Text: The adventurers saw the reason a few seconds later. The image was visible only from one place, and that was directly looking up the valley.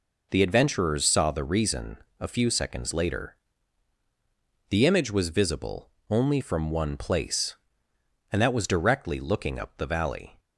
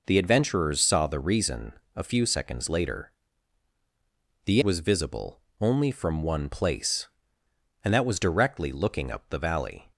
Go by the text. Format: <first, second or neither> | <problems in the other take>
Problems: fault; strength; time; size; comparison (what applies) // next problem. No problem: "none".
first | pauses between "reason" and "a"; slight; at 1.7 s; 0.22 s long; slight in the first // skips "image"; at 4.6 s // pauses between "visible" and "only"; slight; at 5.3 s; 0.20 s long; slight in the first